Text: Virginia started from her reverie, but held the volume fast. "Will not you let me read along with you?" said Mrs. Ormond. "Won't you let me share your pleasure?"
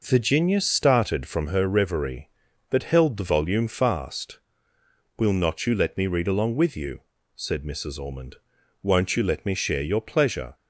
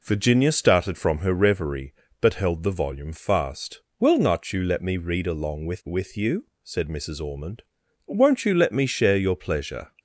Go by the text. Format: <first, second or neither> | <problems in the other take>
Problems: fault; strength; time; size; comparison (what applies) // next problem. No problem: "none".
first | says "with" twice; at 5.8 s